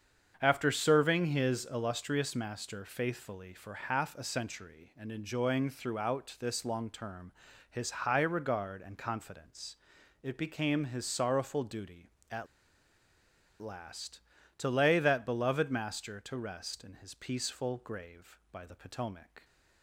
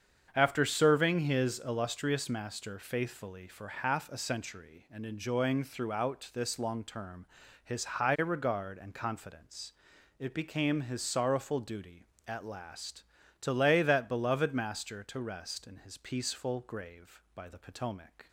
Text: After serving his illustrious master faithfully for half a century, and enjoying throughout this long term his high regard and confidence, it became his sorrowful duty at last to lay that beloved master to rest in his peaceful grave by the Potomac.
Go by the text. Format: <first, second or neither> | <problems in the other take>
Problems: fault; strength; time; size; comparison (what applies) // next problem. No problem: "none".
second | starts louder than the rest; strong; until 1.4 s; 7.5 dB; strong in the second // pauses between "term" and "his"; at 7.3 s; 0.38 s long; also in the second // pauses between "at" and "last"; at 12.4 s; 1.1 s long